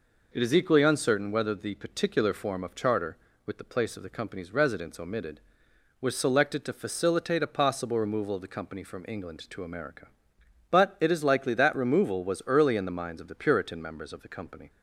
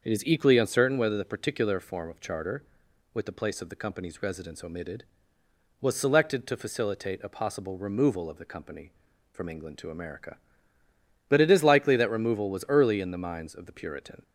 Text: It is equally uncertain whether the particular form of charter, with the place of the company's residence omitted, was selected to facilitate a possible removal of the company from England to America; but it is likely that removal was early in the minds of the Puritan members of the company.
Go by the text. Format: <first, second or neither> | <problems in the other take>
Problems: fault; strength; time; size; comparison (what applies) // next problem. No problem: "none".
first | starts louder than the rest; until 1.0 s; 6.5 dB // stops before "members of the company"; at 14.2 s